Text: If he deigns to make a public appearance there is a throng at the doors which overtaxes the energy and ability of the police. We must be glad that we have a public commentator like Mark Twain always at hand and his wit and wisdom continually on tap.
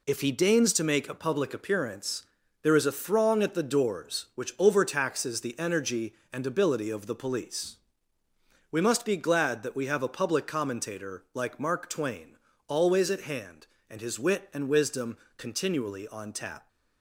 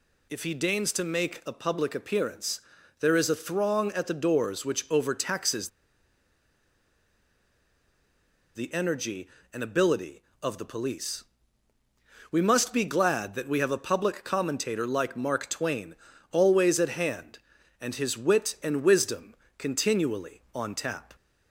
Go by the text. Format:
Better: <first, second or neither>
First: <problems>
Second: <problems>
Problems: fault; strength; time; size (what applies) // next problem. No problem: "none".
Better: first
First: pauses between "appearance" and "there"; slight; at 2.2 s; 0.36 s long // pauses between "Twain" and "always"; slight; at 12.3 s; 0.32 s long // pauses between "wisdom" and "continually"; slight; at 15.1 s; 0.20 s long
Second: pauses between "appearance" and "there"; at 2.6 s; 0.40 s long // pauses between "overtaxes" and "the"; strong; at 5.6 s; 2.8 s long // pauses between "Twain" and "always"; slight; at 15.9 s; 0.36 s long // pauses between "wisdom" and "continually"; slight; at 19.3 s; 0.22 s long